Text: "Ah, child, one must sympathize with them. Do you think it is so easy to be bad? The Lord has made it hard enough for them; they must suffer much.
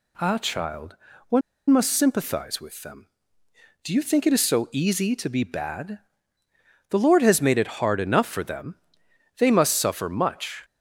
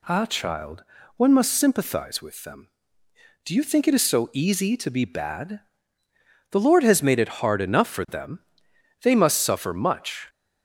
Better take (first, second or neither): second